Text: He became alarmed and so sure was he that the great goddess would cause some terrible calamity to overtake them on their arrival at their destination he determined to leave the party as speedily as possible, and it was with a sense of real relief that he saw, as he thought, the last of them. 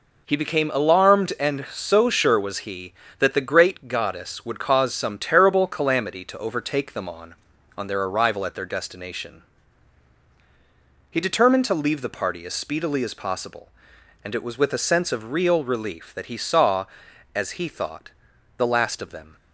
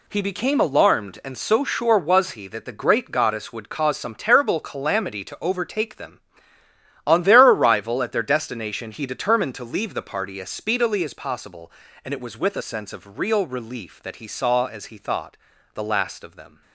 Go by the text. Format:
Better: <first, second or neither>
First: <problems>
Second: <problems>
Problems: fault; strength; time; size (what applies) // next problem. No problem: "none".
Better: second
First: says "on" twice; at 7.7 s // pauses between "destination" and "he"; strong; at 9.4 s; 1.7 s long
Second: none